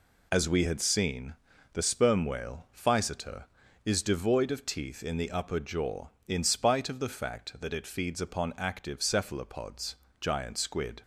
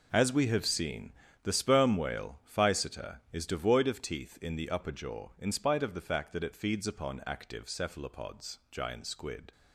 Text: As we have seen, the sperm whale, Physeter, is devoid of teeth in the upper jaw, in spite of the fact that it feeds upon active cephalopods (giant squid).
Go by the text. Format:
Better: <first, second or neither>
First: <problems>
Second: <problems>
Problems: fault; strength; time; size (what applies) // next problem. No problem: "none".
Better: second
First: says "had" for "have"; at 0.6 s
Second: none